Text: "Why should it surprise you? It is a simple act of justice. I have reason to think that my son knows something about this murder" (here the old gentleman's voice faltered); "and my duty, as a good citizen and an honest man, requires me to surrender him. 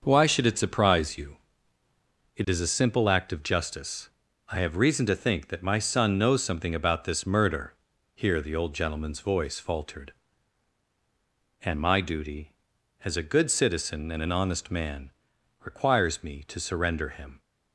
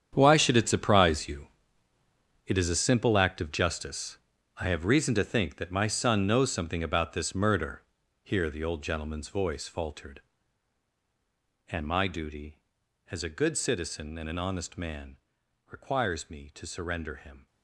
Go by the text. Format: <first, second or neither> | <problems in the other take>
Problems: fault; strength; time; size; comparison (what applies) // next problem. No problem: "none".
first | gets quieter; strong; throughout; 13.5 dB // starts louder than the rest; strong; until 1.1 s; 8.5 dB; noticeable in the first